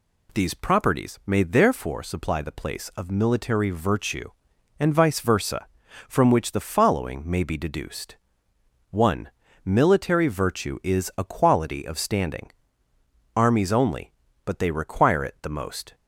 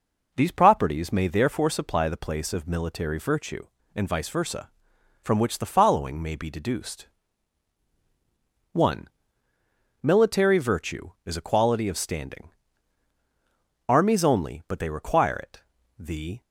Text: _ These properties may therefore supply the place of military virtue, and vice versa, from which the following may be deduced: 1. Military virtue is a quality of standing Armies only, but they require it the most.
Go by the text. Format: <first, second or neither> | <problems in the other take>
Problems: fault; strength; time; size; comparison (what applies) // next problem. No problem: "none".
first | pauses between "standing" and "Armies"; strong; at 12.4 s; 1.4 s long; noticeable in the first // pauses between "it" and "the"; slight; at 15.6 s; 0.36 s long // stops before "most"; at 16.4 s